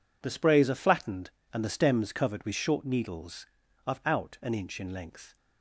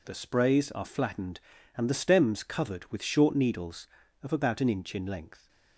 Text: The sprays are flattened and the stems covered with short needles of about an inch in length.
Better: second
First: says "out" for "about"; at 4.0 s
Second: none

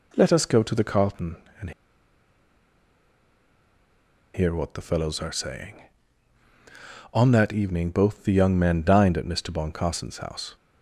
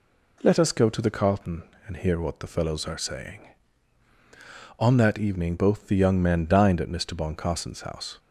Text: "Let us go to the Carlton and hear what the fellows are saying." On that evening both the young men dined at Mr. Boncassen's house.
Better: second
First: pauses between "and" and "hear"; strong; at 1.7 s; 2.6 s long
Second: none

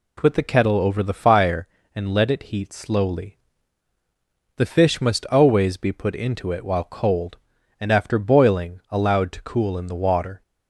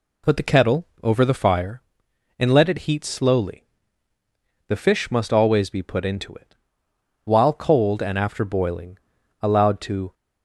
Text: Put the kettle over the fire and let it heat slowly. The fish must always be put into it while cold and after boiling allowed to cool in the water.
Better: first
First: none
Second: pauses between "kettle" and "over"; slight; at 0.8 s; 0.16 s long // pauses between "it" and "while"; noticeable; at 6.5 s; 0.70 s long // pauses between "boiling" and "allowed"; at 8.9 s; 0.44 s long // stops before "cool in the water"; at 10.1 s

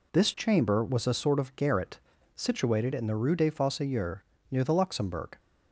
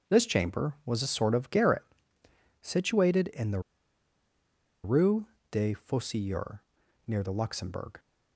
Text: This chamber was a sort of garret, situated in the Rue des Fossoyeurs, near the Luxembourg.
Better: first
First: none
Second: starts louder than the rest; until 1.1 s; 7 dB // pauses between "the" and "Rue"; at 3.5 s; 1.2 s long // pauses between "Rue" and "des"; slight; at 5.2 s; 0.24 s long

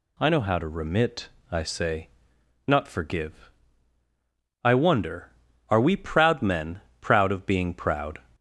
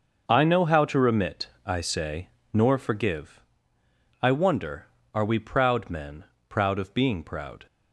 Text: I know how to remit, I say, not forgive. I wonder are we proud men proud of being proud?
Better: first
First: pauses between "men" and "proud"; slight; at 6.8 s; 0.20 s long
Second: starts louder than the rest; until 1.2 s; 6 dB // says "nor" for "not"; at 2.5 s // pauses between "men" and "proud"; slight; at 6.2 s; 0.24 s long

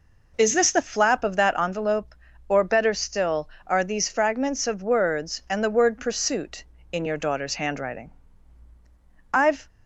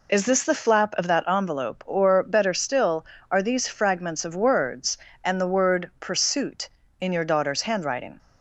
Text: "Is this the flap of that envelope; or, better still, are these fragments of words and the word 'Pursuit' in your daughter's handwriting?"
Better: second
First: goes on to say "I've"; slight; from 9.3 s on; 0.34 s long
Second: none

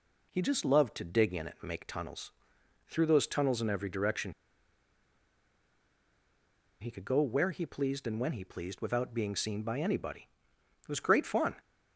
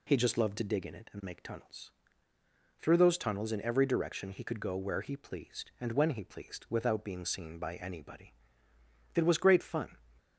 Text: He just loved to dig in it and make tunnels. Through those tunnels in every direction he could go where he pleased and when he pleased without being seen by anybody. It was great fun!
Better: second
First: pauses between "direction" and "he"; strong; at 4.3 s; 2.4 s long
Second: none

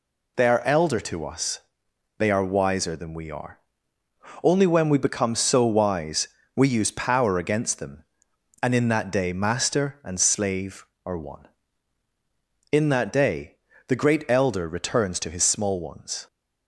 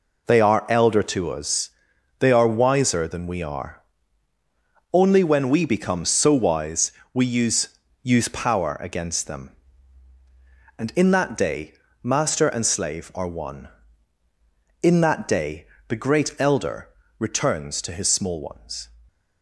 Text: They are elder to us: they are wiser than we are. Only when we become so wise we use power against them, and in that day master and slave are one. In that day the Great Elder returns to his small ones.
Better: first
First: pauses between "wise" and "we"; slight; at 6.2 s; 0.30 s long // pauses between "day" and "the"; slight; at 13.5 s; 0.28 s long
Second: pauses between "wise" and "we"; slight; at 6.9 s; 0.22 s long // says "use" twice; at 8.0 s // pauses between "day" and "master"; slight; at 11.7 s; 0.28 s long // pauses between "day" and "the"; slight; at 15.6 s; 0.22 s long // pauses between "Elder" and "returns"; slight; at 16.8 s; 0.30 s long

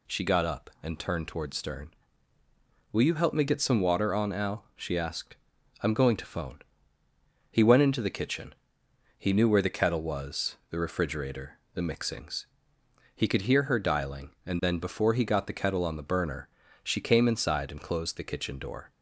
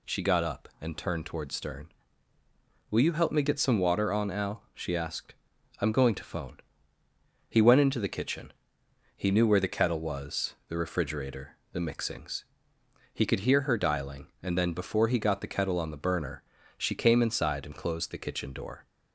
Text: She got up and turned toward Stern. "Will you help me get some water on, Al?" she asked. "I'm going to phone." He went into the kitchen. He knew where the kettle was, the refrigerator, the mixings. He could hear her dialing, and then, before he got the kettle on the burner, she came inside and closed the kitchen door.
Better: neither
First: none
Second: none

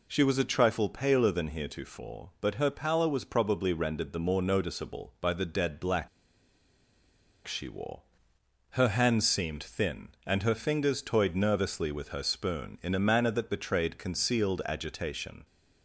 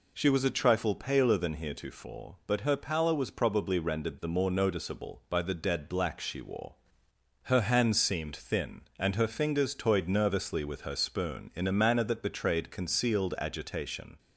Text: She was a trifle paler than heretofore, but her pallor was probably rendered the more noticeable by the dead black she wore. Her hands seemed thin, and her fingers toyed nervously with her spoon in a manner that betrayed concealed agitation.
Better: second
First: pauses between "black" and "she"; strong; at 6.0 s; 1.3 s long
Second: none

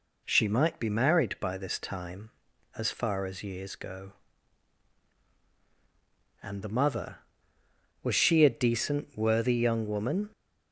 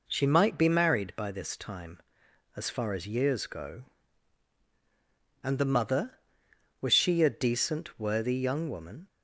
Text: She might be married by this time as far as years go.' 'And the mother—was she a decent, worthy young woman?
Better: neither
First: none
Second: none

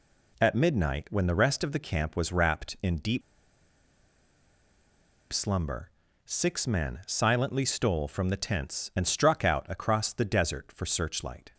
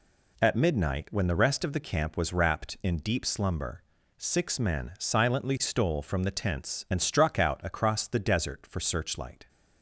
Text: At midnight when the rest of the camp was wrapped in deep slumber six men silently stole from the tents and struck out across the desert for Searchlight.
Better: second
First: pauses between "deep" and "slumber"; strong; at 3.2 s; 2.1 s long // pauses between "slumber" and "six"; slight; at 5.8 s; 0.36 s long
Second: pauses between "slumber" and "six"; slight; at 3.8 s; 0.36 s long

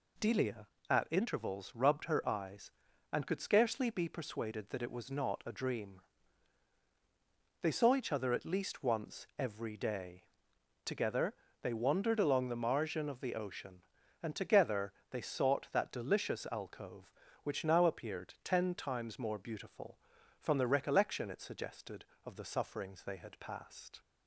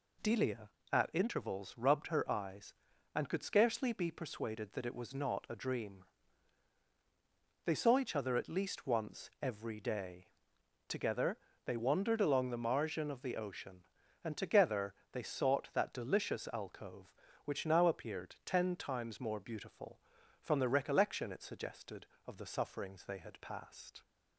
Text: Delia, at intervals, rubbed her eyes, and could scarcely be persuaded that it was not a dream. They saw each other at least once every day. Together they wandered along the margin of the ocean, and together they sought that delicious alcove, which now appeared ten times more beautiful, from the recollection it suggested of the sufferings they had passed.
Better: neither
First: pauses between "Together" and "they"; slight; at 11.3 s; 0.28 s long // pauses between "together" and "they"; slight; at 14.9 s; 0.18 s long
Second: pauses between "Together" and "they"; slight; at 11.3 s; 0.28 s long // pauses between "together" and "they"; slight; at 14.9 s; 0.18 s long

